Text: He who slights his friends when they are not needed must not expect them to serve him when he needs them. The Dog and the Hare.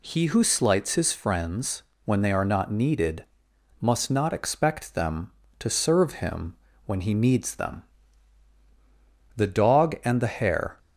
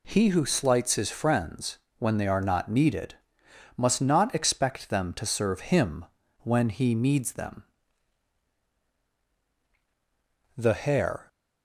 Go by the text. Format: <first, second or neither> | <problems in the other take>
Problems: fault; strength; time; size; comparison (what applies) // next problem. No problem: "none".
first | pauses between "friends" and "when"; slight; at 1.7 s; 0.18 s long; slight in the first // pauses between "needed" and "must"; noticeable; at 3.1 s; 0.60 s long; noticeable in the first // pauses between "him" and "when"; at 6.0 s; 0.38 s long; slight in the first // skips "The Dog and"; at 9.0 s